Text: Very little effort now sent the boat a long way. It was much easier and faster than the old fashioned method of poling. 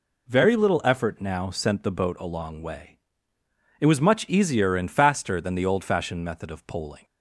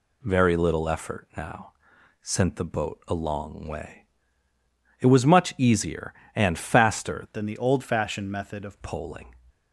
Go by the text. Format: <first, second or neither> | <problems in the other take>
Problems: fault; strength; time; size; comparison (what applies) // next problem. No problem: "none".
first | pauses between "now" and "sent"; noticeable; at 1.7 s; 0.48 s long // changes voice from "than" to "of"; from 7.3 to 8.7 s; 1.4 s long